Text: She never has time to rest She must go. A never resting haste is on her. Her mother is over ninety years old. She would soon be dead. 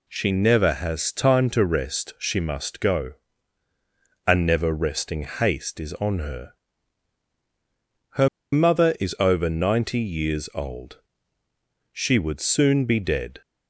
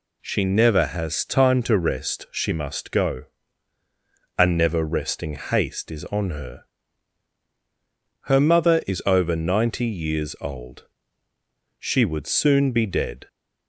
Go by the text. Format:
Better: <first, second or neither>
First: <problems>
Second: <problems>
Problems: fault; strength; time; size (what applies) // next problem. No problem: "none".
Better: second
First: pauses between "Her" and "mother"; slight; at 8.2 s; 0.24 s long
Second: none